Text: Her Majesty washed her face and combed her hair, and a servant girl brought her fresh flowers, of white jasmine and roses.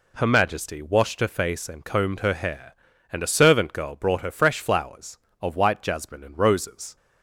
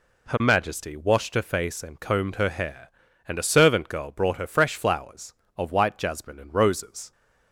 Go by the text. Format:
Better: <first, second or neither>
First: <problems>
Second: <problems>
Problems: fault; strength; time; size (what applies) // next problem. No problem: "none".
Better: neither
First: none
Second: none